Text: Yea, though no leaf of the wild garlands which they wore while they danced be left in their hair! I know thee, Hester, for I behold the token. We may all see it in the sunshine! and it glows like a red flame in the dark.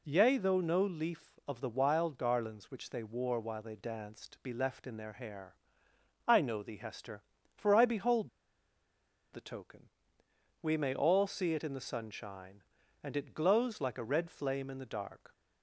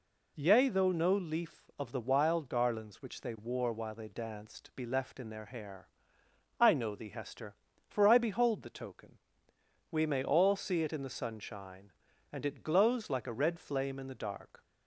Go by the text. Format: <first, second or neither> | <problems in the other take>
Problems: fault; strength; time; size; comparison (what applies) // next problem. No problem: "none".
second | pauses between "behold" and "the"; at 8.2 s; 1.0 s long